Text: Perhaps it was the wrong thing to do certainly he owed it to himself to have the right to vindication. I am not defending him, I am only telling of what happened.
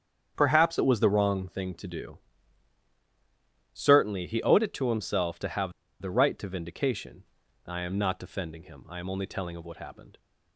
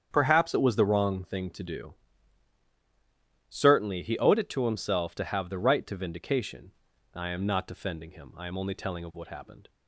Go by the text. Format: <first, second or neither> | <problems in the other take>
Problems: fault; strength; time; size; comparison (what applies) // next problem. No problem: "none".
second | starts louder than the rest; strong; until 1.3 s; 8 dB; strong in the second // pauses between "do" and "certainly"; strong; at 2.1 s; 1.6 s long; strong in the second // pauses between "have" and "the"; slight; at 5.7 s; 0.29 s long